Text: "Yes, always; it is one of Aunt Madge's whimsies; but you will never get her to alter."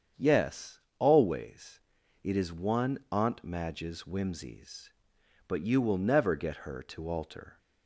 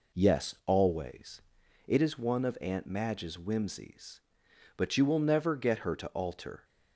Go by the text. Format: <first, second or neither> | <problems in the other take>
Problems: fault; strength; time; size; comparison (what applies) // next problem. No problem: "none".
second | starts louder than the rest; strong; until 1.3 s; 8 dB // skips "of"; at 3.0 s